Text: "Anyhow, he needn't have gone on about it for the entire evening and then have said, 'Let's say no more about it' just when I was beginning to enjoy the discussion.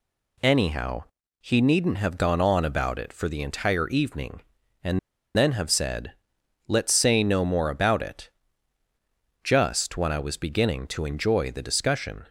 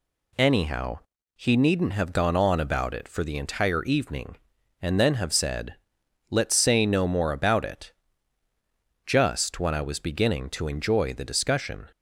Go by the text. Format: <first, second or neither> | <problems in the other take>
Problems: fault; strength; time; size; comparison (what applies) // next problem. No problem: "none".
second | pauses between "and" and "then"; at 4.9 s; 0.37 s long // pauses between "it" and "just"; at 8.3 s; 1.1 s long; also in the second